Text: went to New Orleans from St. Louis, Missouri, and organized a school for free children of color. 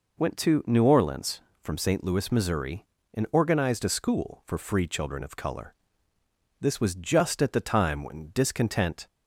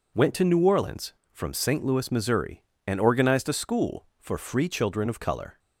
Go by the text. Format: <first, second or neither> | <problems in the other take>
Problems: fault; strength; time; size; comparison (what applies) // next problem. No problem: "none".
second | goes on to say "This was just at the time when discontent"; strong; from 6.6 s on; 2.4 s long